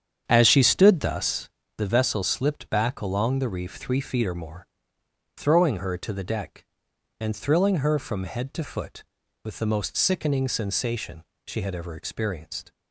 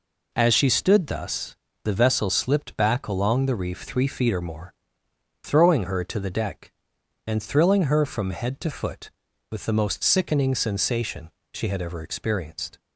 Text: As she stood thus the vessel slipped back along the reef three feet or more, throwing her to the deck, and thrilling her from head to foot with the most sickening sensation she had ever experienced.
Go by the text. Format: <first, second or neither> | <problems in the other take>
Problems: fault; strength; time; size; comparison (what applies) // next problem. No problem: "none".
second | starts louder than the rest; strong; until 1.6 s; 8 dB // pauses between "thus" and "the"; slight; at 1.4 s; 0.28 s long; slight in the second // pauses between "sensation" and "she"; slight; at 11.2 s; 0.22 s long; slight in the second